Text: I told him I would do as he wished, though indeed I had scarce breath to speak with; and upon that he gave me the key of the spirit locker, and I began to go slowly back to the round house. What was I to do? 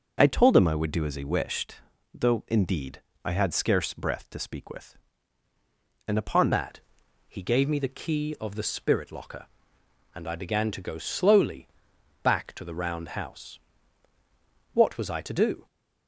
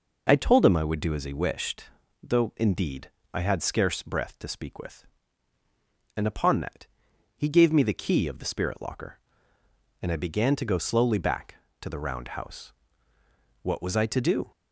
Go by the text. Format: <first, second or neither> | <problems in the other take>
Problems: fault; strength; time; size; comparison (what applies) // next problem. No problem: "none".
second | pauses between "indeed" and "I"; slight; at 3.0 s; 0.22 s long; slight in the second // changes voice at "that"; from 6.5 s on; 9.1 s long // pauses between "that" and "he"; noticeable; at 6.7 s; 0.50 s long; noticeable in the second // pauses between "slowly" and "back"; noticeable; at 11.6 s; 0.58 s long